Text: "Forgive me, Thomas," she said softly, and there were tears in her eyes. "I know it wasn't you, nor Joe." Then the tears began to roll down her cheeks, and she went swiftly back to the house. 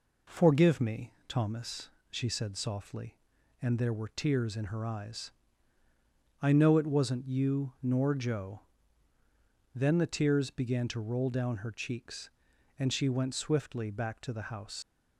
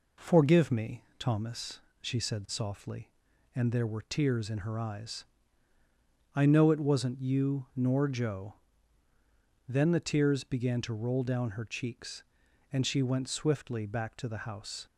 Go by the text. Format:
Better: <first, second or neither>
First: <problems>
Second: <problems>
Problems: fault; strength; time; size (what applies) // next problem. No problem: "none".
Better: second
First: leaves "house" unfinished; at 14.8 s; 80 ms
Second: none